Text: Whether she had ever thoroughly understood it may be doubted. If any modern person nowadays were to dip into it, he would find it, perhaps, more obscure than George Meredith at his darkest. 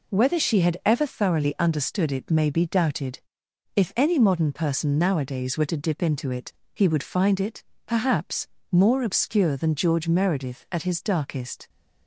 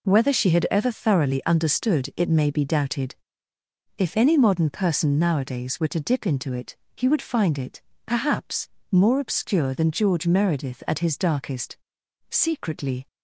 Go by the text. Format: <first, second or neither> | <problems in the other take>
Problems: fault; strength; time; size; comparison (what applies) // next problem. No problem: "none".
first | goes on to say "Secretly"; noticeable; from 12.2 s on; 0.78 s long